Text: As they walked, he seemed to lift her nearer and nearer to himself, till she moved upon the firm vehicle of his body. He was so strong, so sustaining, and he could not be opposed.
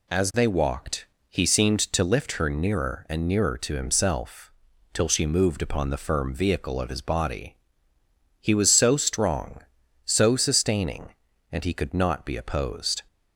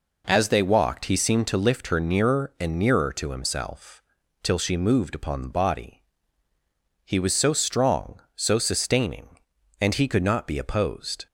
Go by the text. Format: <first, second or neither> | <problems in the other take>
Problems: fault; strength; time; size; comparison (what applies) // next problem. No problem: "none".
first | skips "firm vehicle of his"; at 5.4 s